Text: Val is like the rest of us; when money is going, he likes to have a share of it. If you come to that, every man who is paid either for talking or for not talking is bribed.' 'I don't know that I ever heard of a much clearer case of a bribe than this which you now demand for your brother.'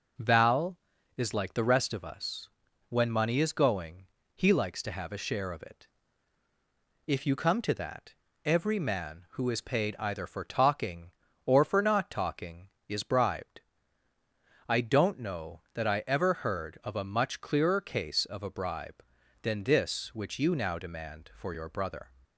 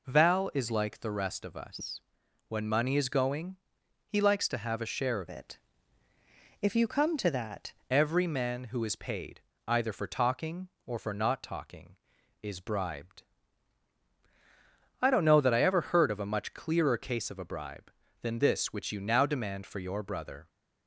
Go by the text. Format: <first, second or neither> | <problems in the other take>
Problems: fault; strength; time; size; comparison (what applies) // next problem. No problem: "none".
first | changes voice from "it" to "that"; from 5.2 to 7.7 s; 2.5 s long // pauses between "paid" and "either"; slight; at 9.4 s; 0.26 s long